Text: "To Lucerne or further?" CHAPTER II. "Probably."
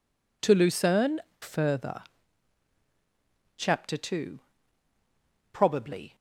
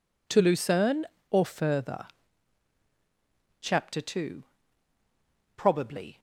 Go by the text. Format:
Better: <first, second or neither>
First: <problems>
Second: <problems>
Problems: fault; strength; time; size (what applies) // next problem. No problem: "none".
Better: second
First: skips "or"; at 1.3 s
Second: none